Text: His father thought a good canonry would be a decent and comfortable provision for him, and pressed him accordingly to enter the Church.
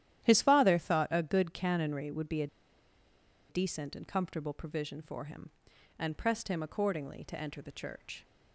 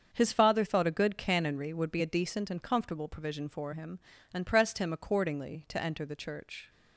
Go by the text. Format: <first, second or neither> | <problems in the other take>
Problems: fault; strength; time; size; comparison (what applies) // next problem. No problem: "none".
second | starts louder than the rest; strong; until 1.2 s; 11.5 dB; also in the second // pauses between "a" and "decent"; at 2.4 s; 1.0 s long